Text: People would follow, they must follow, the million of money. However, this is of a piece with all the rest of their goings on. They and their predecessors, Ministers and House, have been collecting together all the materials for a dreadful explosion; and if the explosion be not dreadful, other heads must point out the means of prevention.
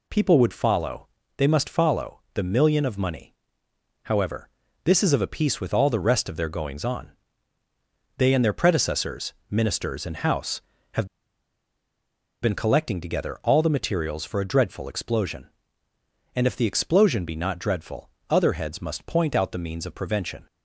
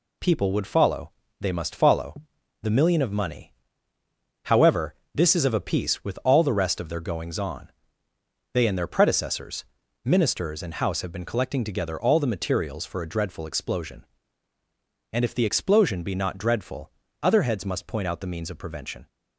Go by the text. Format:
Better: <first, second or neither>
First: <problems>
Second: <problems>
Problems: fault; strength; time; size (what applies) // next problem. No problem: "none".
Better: second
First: pauses between "have" and "been"; strong; at 11.0 s; 1.3 s long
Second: none